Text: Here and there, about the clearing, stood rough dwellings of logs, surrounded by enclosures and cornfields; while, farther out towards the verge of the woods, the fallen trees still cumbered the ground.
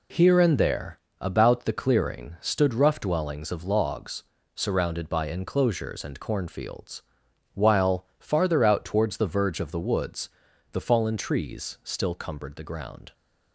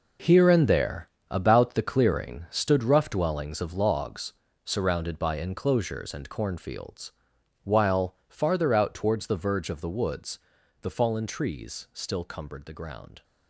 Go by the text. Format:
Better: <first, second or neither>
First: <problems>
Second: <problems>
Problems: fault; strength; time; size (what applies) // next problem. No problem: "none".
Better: first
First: none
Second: gets quieter; strong; throughout; 11.5 dB